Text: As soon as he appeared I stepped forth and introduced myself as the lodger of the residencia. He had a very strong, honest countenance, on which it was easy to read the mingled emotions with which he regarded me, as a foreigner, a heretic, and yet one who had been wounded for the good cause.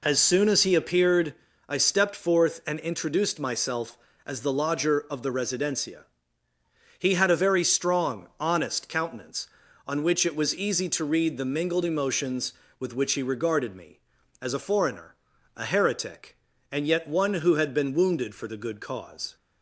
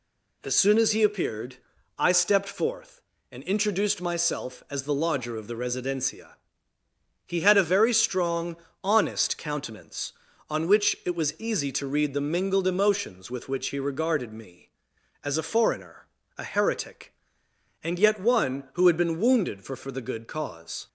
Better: first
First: pauses between "appeared" and "I"; slight; at 1.3 s; 0.32 s long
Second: pauses between "appeared" and "I"; at 1.5 s; 0.40 s long // says "for" twice; at 19.7 s

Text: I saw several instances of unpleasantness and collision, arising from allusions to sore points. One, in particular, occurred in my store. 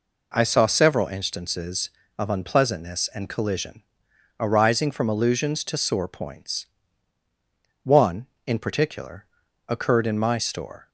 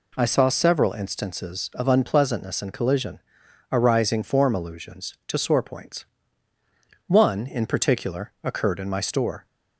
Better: first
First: none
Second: says "form" for "from"; at 4.2 s

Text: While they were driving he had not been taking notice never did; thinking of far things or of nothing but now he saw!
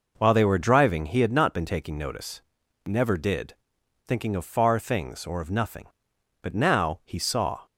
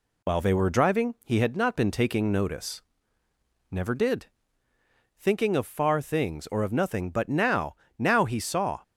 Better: first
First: pauses between "notice" and "never"; noticeable; at 2.4 s; 0.46 s long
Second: pauses between "notice" and "never"; noticeable; at 2.8 s; 0.90 s long // says "now" twice; at 7.9 s

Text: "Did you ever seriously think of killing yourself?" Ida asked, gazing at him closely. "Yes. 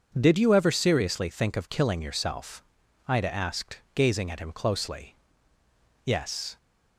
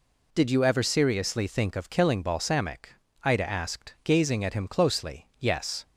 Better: first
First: none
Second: says "balsamic" for "yourself"; at 2.2 s

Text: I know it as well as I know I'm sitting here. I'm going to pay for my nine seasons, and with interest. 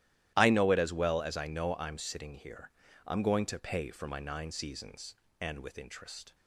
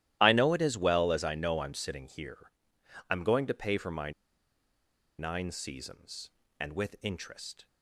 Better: first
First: starts louder than the rest; strong; until 1.3 s; 13.5 dB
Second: starts louder than the rest; strong; until 1.2 s; 13.5 dB // pauses between "my" and "nine"; at 4.1 s; 1.0 s long

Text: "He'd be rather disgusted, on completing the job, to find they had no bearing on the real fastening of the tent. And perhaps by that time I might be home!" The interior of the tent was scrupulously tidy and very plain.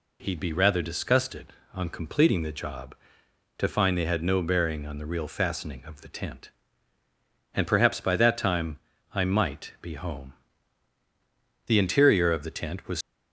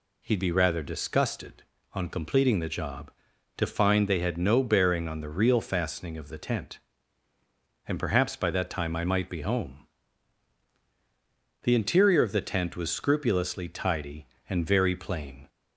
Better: second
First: pauses between "time" and "I"; slight; at 8.7 s; 0.36 s long // stops before "scrupulously tidy and very plain"; at 13.0 s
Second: none

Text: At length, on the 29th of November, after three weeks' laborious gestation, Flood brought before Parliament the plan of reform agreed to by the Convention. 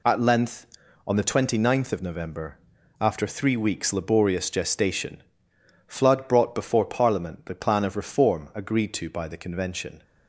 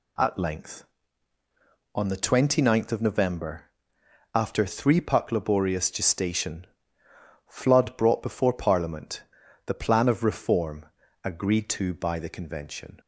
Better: first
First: none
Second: says "puck" for "weeks"; at 4.9 s // pauses between "Parliament" and "the"; noticeable; at 9.2 s; 0.46 s long // pauses between "reform" and "agreed"; slight; at 10.8 s; 0.36 s long

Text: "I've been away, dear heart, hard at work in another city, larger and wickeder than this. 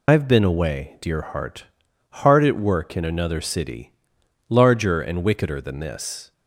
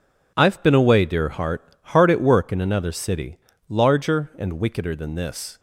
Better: second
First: loses the start of "I've"; at 0.0 s; 60 ms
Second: none

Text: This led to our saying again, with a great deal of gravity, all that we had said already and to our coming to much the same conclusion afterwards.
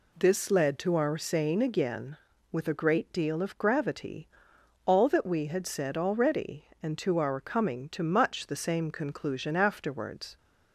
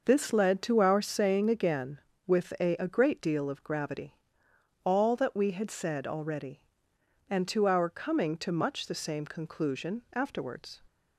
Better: first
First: none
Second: says "a" twice; at 2.7 s

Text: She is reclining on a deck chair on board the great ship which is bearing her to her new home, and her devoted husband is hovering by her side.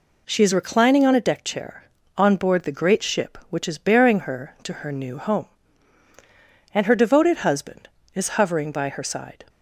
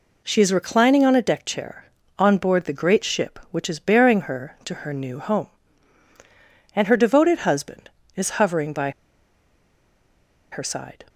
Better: first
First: none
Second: pauses between "by" and "her"; strong; at 8.9 s; 1.6 s long

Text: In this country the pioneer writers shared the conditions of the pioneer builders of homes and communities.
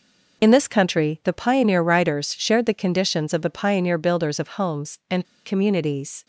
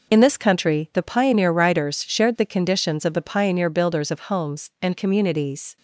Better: second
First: pauses between "and" and "communities"; slight; at 5.2 s; 0.20 s long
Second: none

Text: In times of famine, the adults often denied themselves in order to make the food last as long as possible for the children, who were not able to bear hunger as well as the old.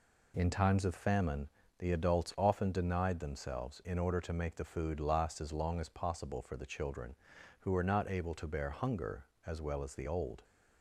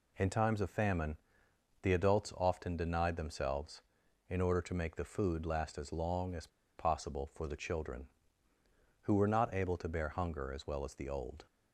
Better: first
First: none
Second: pauses between "as" and "possible"; slight; at 6.4 s; 0.30 s long

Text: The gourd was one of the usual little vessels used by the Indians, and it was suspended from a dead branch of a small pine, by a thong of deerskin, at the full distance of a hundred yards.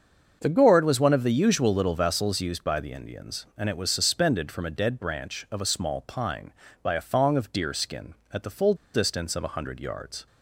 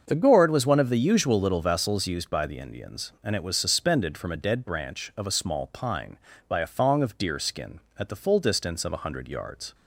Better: second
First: starts louder than the rest; until 1.4 s; 6.5 dB // pauses between "full" and "distance"; slight; at 8.7 s; 0.18 s long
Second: starts louder than the rest; until 1.0 s; 6.5 dB

